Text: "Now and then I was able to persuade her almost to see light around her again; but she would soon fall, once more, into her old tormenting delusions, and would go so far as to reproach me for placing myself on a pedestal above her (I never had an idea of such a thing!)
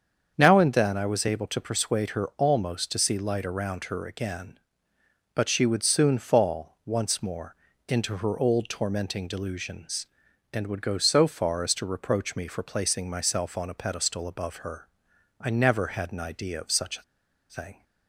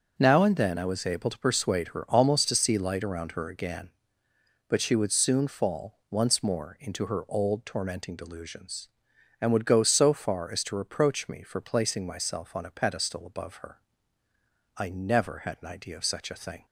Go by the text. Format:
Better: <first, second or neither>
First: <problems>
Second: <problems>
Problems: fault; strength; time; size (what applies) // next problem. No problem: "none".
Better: second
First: starts louder than the rest; strong; until 1.3 s; 7 dB // pauses between "a" and "thing"; noticeable; at 17.0 s; 0.47 s long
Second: starts louder than the rest; noticeable; until 1.1 s; 6 dB